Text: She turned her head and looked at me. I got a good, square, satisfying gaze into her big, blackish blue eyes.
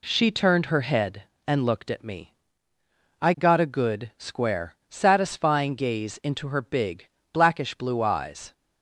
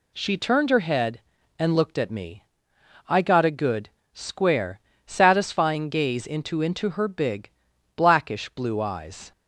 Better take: first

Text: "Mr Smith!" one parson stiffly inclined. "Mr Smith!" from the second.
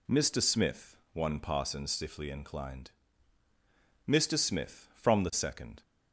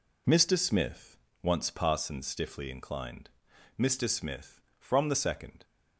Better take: first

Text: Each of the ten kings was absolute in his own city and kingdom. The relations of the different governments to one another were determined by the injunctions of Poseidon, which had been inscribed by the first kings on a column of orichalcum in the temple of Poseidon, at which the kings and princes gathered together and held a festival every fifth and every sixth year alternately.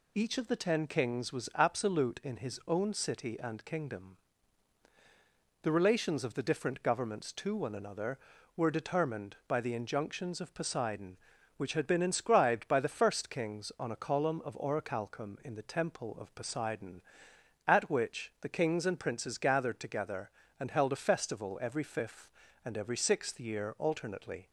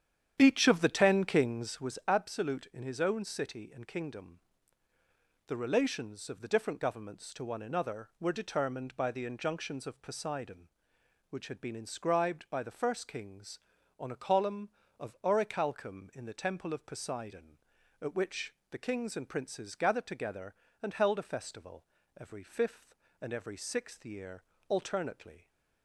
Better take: first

